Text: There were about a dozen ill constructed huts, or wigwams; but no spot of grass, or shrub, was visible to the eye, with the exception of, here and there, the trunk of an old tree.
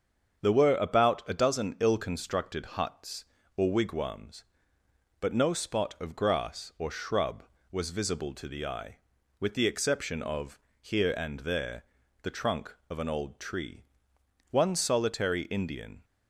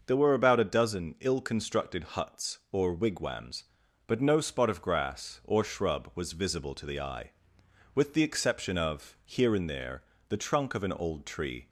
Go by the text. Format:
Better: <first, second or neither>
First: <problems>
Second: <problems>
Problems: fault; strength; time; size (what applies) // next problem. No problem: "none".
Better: second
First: starts louder than the rest; until 1.4 s; 7 dB // goes on to say "One solitary Indian"; from 14.5 s on; 1.5 s long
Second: starts louder than the rest; noticeable; until 1.0 s; 6 dB